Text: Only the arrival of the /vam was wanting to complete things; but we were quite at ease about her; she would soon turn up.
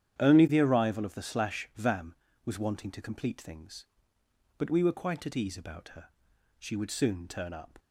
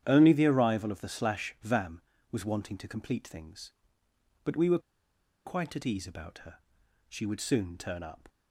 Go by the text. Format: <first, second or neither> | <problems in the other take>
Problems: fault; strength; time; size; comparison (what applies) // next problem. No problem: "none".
first | starts louder than the rest; strong; until 1.0 s; 10 dB; strong in the first // pauses between "were" and "quite"; noticeable; at 4.7 s; 0.66 s long